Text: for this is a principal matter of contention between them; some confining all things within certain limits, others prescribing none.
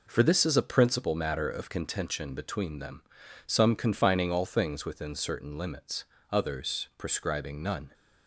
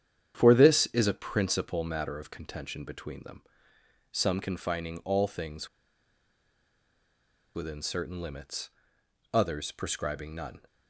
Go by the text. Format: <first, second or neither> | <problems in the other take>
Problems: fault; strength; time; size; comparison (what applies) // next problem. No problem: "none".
first | starts louder than the rest; strong; until 1.3 s; 9 dB // pauses between "things" and "within"; strong; at 5.6 s; 1.8 s long